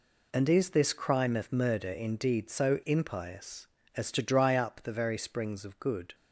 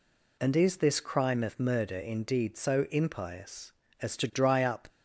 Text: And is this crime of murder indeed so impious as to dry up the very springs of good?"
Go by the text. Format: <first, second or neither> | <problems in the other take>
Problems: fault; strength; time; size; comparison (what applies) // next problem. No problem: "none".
first | stops before "the very springs of good"; at 4.8 s